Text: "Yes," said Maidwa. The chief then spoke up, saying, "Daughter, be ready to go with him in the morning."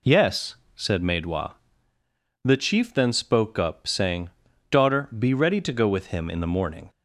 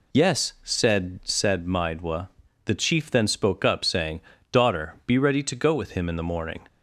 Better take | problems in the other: first | says "said" twice; at 1.2 s

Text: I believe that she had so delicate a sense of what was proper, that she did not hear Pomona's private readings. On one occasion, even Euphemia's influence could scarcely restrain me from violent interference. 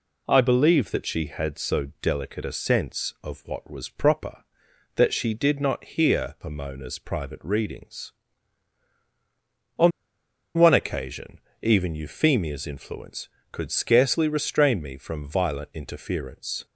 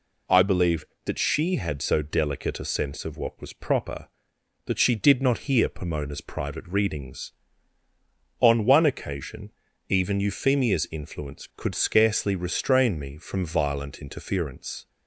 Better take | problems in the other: second | pauses between "On" and "one"; noticeable; at 9.9 s; 0.66 s long

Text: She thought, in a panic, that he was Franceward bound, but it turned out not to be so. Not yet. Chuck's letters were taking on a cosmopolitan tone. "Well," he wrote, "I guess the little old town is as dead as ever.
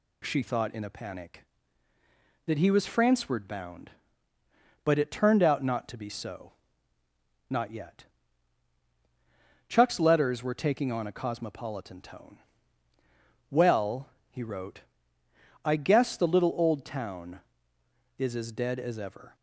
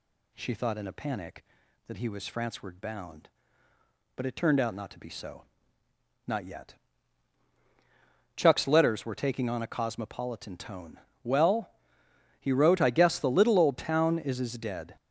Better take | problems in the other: first | stops before "as ever"; at 14.9 s

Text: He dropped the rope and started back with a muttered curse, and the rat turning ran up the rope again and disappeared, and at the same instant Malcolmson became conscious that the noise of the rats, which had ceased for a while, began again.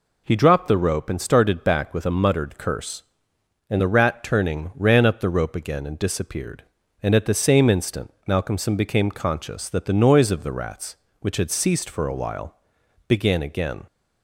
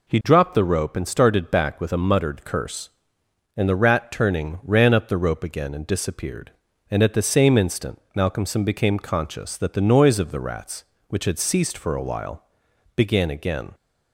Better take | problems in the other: neither | pauses between "instant" and "Malcolmson"; slight; the same in both

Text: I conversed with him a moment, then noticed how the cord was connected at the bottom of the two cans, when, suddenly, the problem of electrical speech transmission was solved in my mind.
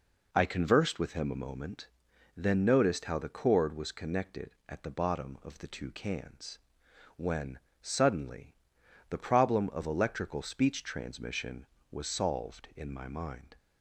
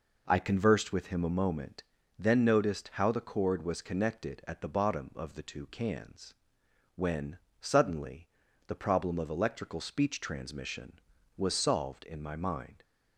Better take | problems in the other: neither | none

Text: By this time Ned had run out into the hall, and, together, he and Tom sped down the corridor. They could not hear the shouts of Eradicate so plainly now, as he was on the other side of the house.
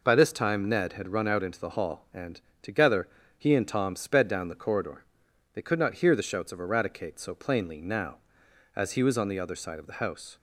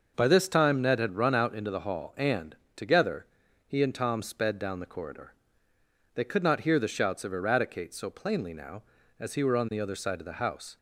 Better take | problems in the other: first | starts louder than the rest; noticeable; until 1.1 s; 6 dB // says "were" for "was"; at 9.4 s

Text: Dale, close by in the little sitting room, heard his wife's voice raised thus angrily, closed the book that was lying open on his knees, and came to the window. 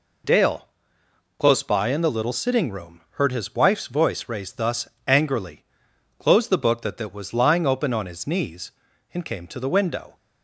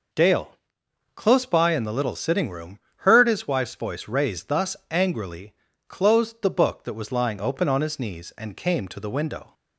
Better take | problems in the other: second | pauses between "thus" and "angrily"; slight; at 4.8 s; 0.20 s long // says "that" twice; at 6.9 s

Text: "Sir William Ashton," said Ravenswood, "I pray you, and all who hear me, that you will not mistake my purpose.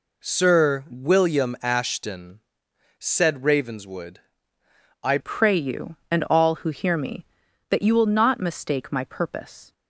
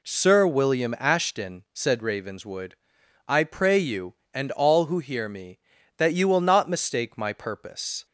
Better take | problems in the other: second | changes voice at "pray"; from 5.1 s on; 4.6 s long

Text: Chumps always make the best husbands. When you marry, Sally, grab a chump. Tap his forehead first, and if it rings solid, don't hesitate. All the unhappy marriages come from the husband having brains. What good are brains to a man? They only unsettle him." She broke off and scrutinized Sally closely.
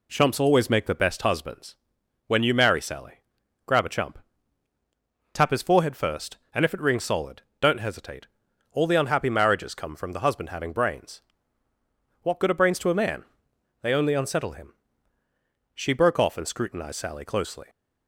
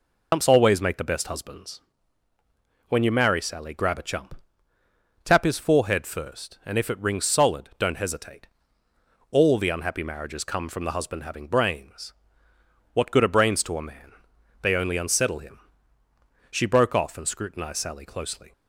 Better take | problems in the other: first | loses the start of "Chumps"; at 0.3 s; 100 ms

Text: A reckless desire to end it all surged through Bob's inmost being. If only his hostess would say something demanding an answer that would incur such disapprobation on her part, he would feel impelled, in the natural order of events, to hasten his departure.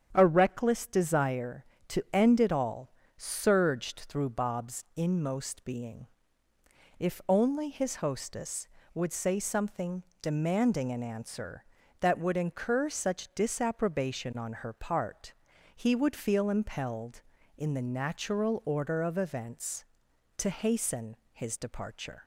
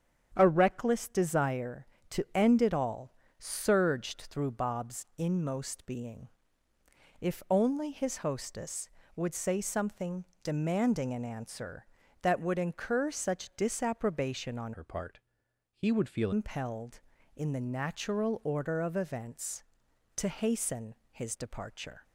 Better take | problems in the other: first | starts louder than the rest; strong; until 1.3 s; 8 dB; strong in the first // pauses between "all" and "surged"; slight; at 3.1 s; 0.24 s long; slight in the first // pauses between "something" and "demanding"; slight; at 10.2 s; 0.18 s long; slight in the first // changes voice from "her" to "feel"; from 14.7 to 16.3 s; 1.6 s long // pauses between "hasten" and "his"; slight; at 20.9 s; 0.18 s long; slight in the first

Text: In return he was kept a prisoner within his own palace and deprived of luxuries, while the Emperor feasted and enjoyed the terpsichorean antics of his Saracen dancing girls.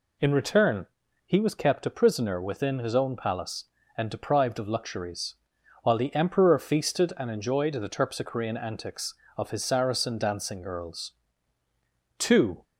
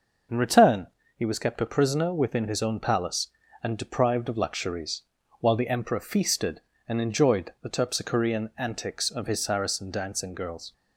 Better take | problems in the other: second | pauses between "return" and "he"; at 0.8 s; 0.40 s long; slight in the second // goes on to say "Two"; slight; from 12.1 s on; 0.46 s long

